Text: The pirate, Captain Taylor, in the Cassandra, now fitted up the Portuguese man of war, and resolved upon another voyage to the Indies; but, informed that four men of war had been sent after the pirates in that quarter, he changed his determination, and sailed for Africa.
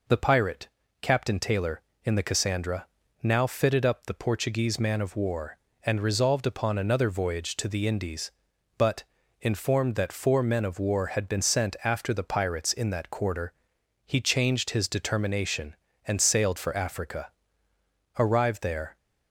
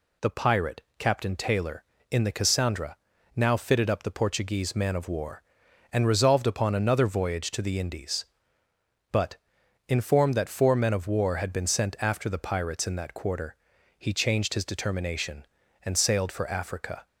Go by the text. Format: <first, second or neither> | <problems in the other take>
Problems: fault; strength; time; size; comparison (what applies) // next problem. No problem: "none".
second | goes on to say "Arrived there"; noticeable; from 18.1 s on; 0.78 s long